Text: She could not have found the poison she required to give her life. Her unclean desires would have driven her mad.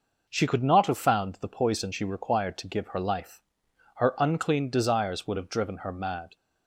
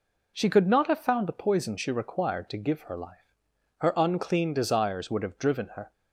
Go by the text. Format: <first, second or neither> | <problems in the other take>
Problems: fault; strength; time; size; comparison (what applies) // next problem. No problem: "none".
first | stops before "mad"; at 5.9 s